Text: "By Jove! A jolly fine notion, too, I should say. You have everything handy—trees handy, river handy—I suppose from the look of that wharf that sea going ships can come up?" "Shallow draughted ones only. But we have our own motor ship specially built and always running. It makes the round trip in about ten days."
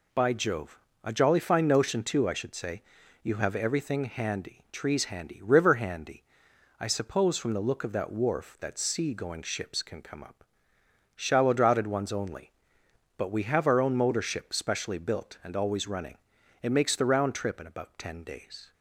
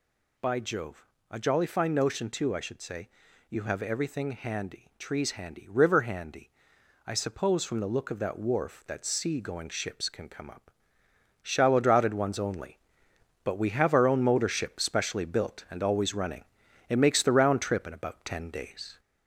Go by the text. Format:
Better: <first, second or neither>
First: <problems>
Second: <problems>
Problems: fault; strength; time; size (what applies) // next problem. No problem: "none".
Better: first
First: none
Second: gets louder; slight; throughout; 3 dB